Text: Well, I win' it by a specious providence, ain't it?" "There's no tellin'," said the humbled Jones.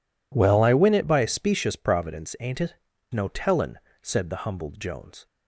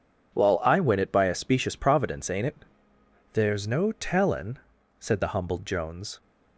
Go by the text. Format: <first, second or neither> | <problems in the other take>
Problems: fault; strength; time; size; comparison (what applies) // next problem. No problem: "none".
second | skips "There's"; at 2.9 s